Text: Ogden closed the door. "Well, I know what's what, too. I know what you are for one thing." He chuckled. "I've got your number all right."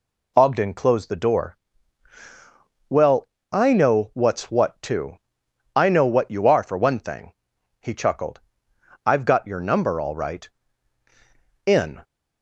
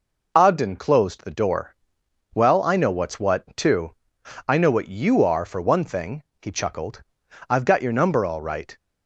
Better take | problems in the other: second | goes on to say "In"; slight; from 11.6 s on; 0.36 s long

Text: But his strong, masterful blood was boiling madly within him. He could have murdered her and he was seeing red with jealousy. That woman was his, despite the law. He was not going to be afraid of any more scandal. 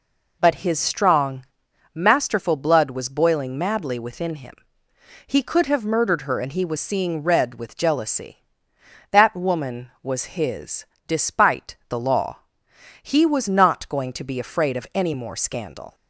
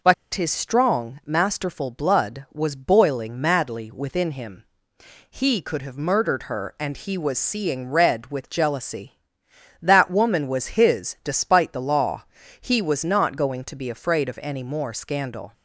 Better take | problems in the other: first | pauses between "But" and "his"; slight; at 0.1 s; 0.20 s long

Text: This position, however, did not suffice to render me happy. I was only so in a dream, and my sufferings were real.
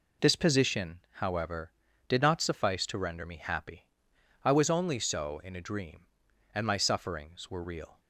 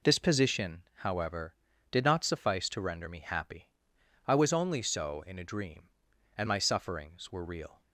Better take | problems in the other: neither | none

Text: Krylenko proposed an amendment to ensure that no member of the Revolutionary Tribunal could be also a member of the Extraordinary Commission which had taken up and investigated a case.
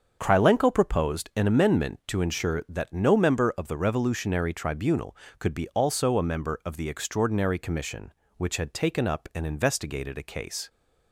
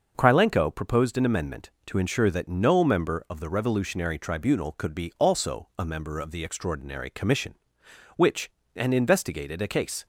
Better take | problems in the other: first | starts louder than the rest; noticeable; until 1.1 s; 6 dB; also in the first // skips "had taken up"; at 8.6 s

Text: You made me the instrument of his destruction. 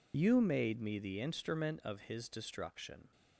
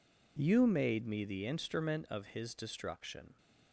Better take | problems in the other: second | loses the start of "You"; at 0.1 s; 40 ms

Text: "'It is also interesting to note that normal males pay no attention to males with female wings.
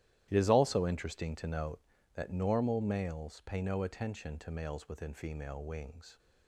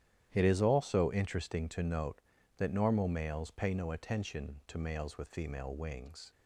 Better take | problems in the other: second | starts louder than the rest; strong; until 1.3 s; 13 dB; strong in the second // says "within" for "with"; at 4.8 s

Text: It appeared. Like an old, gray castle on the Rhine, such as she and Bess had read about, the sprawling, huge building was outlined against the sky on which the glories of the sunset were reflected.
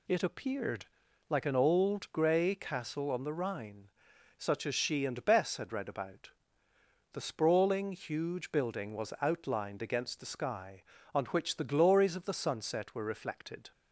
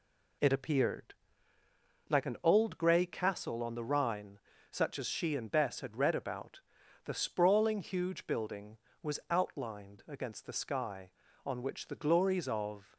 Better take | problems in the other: first | stops before "the sunset were reflected"; at 12.9 s

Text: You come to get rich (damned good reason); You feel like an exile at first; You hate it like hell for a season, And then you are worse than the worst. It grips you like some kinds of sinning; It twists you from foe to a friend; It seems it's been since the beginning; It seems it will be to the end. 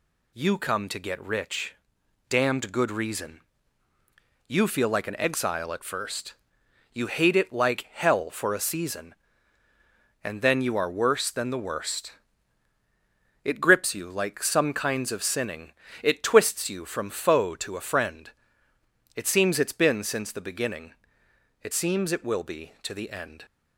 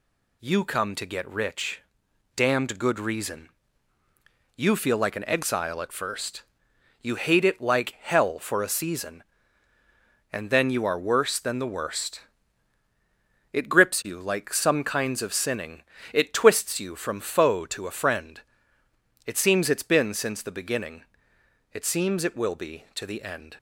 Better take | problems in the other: neither | none

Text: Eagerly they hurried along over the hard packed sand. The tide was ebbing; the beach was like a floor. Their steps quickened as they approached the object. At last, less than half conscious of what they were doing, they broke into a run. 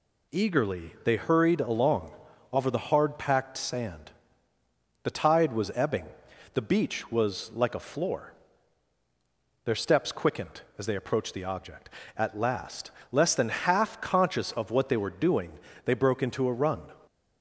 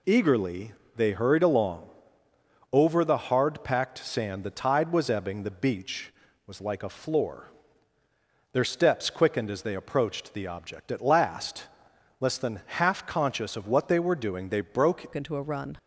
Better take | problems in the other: first | pauses between "Eagerly" and "they"; slight; at 0.7 s; 0.24 s long // pauses between "along" and "over"; noticeable; at 1.8 s; 0.84 s long; also in the first // changes voice at "into"; from 15.1 s on; 0.6 s long

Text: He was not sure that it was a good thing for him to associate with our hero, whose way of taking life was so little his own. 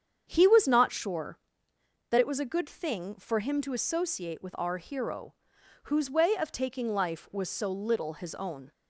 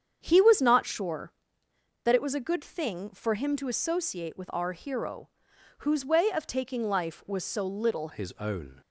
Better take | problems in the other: first | starts louder than the rest; strong; until 1.2 s; 8 dB; strong in the first // changes voice at "his"; from 8.1 s on; 0.7 s long

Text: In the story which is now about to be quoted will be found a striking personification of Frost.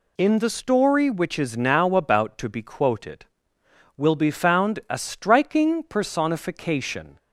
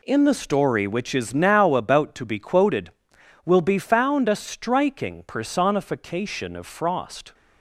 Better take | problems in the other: second | stops before "of Frost"; at 7.1 s

